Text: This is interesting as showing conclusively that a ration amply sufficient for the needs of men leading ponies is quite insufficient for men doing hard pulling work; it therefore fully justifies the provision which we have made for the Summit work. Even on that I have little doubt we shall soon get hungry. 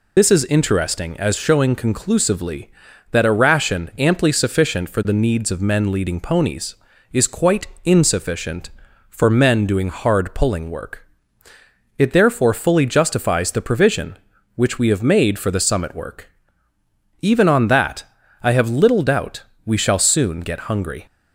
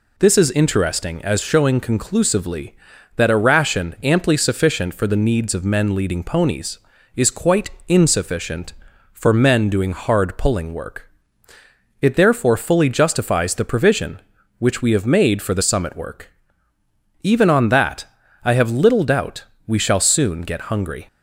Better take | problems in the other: second | loses the start of "This"; at 0.1 s; 50 ms // pauses between "quite" and "insufficient"; slight; at 7.6 s; 0.16 s long; slight in the second // pauses between "that" and "I"; at 18.0 s; 0.40 s long; also in the second // pauses between "doubt" and "we"; slight; at 19.4 s; 0.20 s long; slight in the second

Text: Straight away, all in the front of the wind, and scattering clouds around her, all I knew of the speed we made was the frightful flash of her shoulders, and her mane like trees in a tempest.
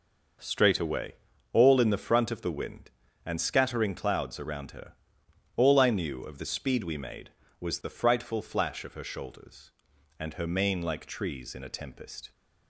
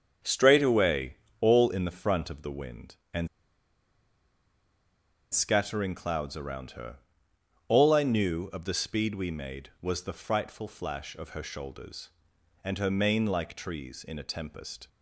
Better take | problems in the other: first | starts louder than the rest; strong; until 1.4 s; 7.5 dB // pauses between "and" and "scattering"; strong; at 3.2 s; 2.0 s long

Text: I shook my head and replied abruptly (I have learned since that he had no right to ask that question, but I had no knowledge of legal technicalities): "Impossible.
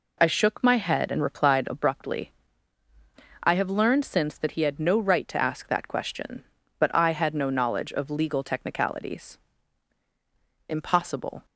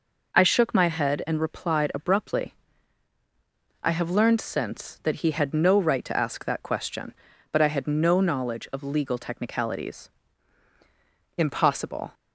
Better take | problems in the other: neither | none

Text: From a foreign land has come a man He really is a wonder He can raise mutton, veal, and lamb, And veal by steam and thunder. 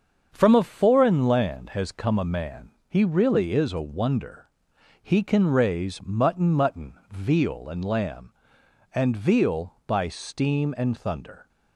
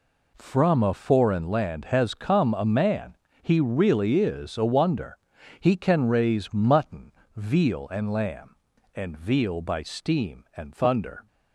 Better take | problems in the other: second | starts louder than the rest; until 1.3 s; 7 dB // pauses between "man" and "He"; slight; at 2.7 s; 0.18 s long; slight in the second // pauses between "wonder" and "He"; noticeable; at 4.4 s; 0.54 s long; also in the second // says "mutton" twice; at 6.5 s

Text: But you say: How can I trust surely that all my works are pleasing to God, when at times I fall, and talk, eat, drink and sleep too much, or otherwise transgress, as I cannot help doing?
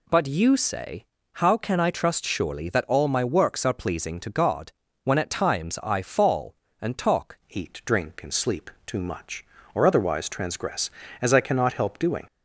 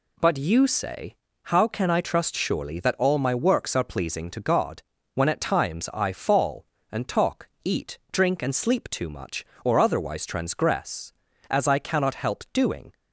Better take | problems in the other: second | changes voice at "eat"; from 7.5 s on; 4.7 s long // pauses between "sleep" and "too"; slight; at 8.6 s; 0.16 s long

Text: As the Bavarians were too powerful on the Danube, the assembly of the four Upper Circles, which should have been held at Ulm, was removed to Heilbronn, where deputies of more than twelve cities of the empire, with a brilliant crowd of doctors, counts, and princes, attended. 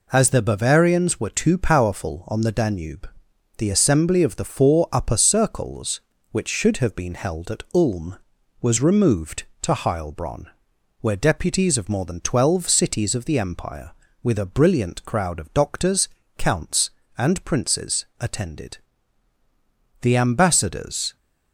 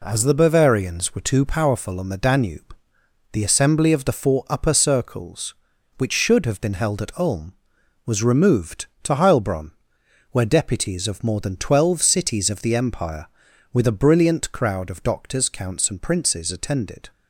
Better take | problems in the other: second | goes on to say "The ambassadors"; noticeable; from 20.0 s on; 1.1 s long

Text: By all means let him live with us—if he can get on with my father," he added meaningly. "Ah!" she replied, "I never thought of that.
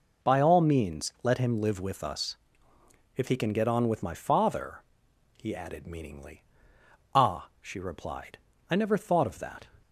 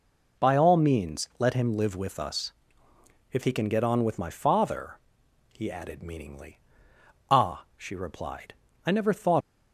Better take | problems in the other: first | stops before "of that"; at 9.4 s

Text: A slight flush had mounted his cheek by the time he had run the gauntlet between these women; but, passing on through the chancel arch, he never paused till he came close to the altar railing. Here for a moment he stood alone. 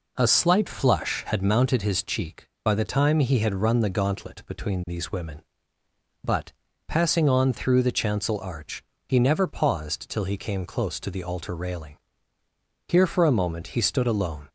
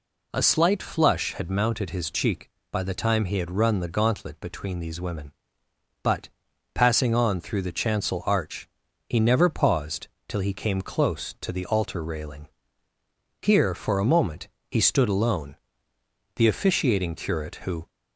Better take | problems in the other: first | pauses between "paused" and "till"; slight; at 10.0 s; 0.22 s long // pauses between "moment" and "he"; slight; at 14.4 s; 0.22 s long // goes on to say "The officiating curate who"; from 16.3 s on; 1.5 s long

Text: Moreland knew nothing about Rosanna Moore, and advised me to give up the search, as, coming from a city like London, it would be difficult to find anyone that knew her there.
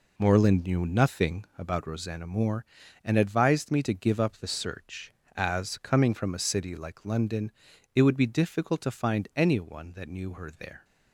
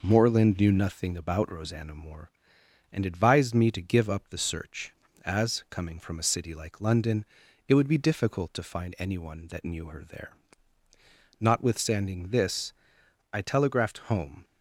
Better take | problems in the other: first | goes on to say "Notwithstanding this I telegraphed home"; strong; from 11.4 s on; 3.0 s long

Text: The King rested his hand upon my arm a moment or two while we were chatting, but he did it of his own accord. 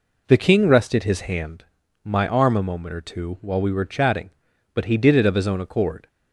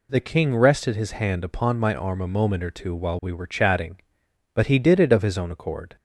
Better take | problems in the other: second | skips "upon"; at 1.8 s

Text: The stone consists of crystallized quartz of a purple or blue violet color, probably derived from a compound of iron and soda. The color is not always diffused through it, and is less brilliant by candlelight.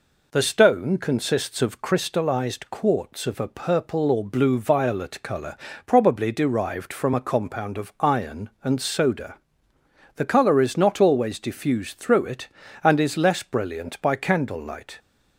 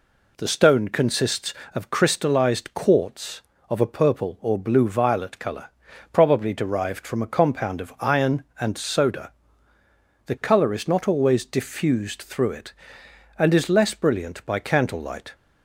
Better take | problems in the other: neither | none

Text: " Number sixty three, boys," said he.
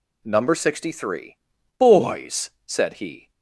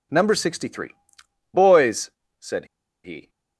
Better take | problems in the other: first | pauses between "said" and "he"; at 2.6 s; 0.39 s long

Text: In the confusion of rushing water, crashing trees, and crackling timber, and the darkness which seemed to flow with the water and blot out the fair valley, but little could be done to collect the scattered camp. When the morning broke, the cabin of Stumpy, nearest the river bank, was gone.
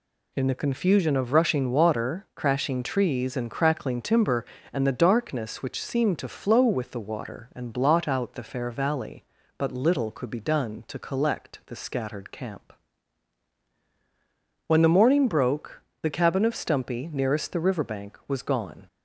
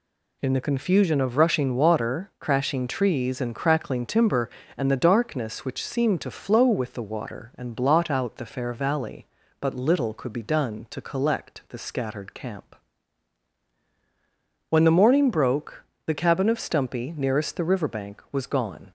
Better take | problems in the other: neither | none

